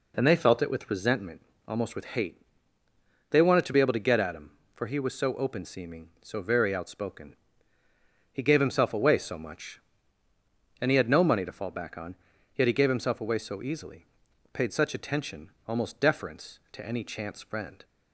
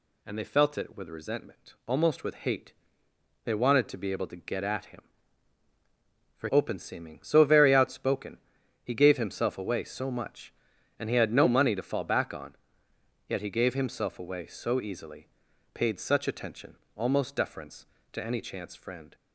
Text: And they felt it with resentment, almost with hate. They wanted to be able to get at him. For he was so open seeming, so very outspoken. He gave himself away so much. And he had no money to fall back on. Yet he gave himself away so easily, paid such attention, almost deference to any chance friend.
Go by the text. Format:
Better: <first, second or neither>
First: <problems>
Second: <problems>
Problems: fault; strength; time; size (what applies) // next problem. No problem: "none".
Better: first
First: none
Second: skips "he was so"; at 6.4 s